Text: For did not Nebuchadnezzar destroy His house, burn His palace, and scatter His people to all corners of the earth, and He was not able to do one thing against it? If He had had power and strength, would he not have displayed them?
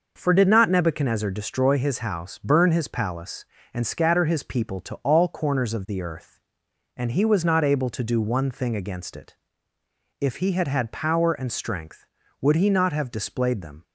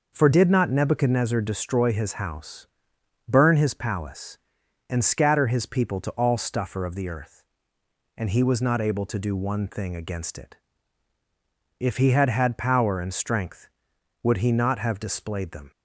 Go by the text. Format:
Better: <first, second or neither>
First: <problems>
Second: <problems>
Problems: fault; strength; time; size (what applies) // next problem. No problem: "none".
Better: first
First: none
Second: says "stuffer" for "corners"; at 6.3 s